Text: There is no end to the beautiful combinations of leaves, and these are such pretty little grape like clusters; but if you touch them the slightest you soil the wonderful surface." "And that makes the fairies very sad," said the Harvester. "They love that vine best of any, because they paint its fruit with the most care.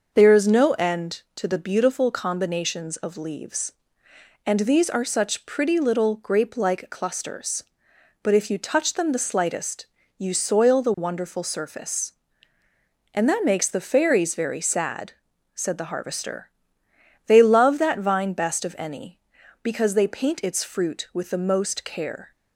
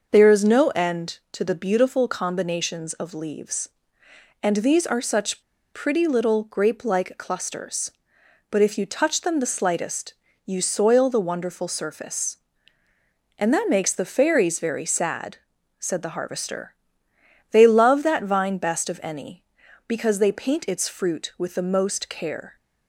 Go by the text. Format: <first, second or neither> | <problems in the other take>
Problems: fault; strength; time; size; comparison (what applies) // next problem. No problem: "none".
first | pauses between "such" and "pretty"; slight; at 5.4 s; 0.31 s long // pauses between "slightest" and "you"; slight; at 10.1 s; 0.32 s long; slight in the first